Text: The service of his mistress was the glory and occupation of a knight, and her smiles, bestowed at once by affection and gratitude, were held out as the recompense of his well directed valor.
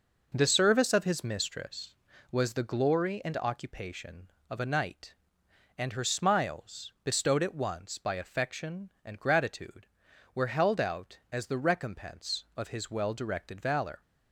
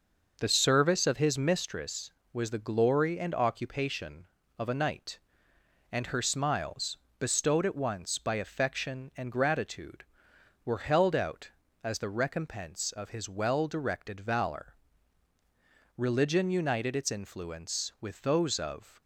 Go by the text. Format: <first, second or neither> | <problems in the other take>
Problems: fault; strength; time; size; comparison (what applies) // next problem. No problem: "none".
first | goes on to say "Religion united its influence with those of"; strong; from 15.9 s on; 3.0 s long